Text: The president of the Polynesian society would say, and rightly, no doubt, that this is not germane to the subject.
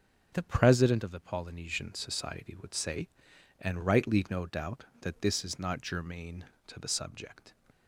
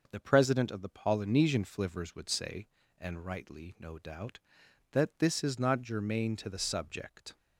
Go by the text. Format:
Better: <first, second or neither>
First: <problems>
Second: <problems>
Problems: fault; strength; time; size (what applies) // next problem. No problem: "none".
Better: first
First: none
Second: starts louder than the rest; noticeable; until 1.1 s; 6 dB // says "flivvers" for "society"; at 1.6 s